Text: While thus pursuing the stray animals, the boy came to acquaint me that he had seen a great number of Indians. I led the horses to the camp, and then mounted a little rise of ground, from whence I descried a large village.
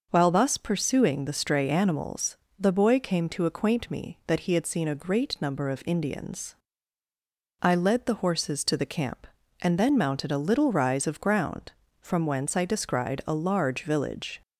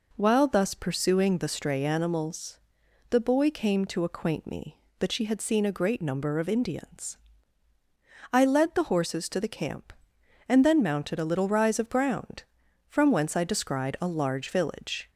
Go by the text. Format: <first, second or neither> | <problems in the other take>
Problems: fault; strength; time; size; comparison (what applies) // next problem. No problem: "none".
first | says "she" for "he"; at 5.1 s